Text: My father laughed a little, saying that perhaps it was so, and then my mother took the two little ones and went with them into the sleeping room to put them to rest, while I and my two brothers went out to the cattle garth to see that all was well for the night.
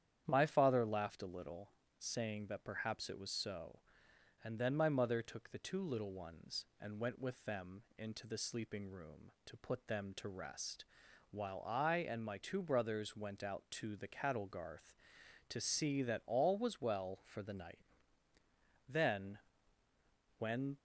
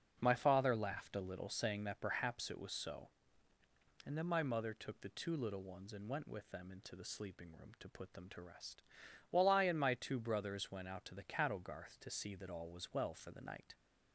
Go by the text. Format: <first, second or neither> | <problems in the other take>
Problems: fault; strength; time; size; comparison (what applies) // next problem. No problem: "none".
second | starts louder than the rest; strong; until 1.2 s; 9.5 dB; noticeable in the second // goes on to say "Then when"; strong; from 18.8 s on; 1.8 s long